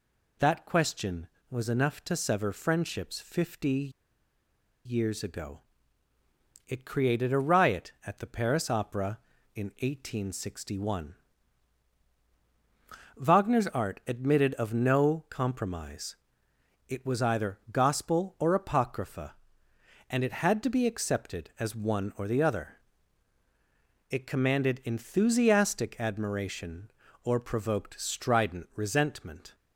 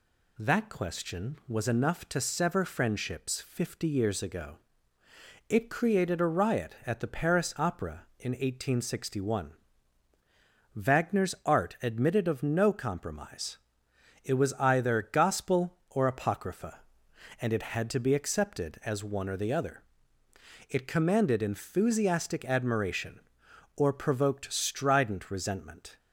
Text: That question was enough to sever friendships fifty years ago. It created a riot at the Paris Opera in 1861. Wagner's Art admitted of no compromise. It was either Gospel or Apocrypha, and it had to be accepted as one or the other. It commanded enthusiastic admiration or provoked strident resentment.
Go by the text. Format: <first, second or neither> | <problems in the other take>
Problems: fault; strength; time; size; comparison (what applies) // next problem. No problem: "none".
second | pauses between "fifty" and "years"; noticeable; at 3.9 s; 0.93 s long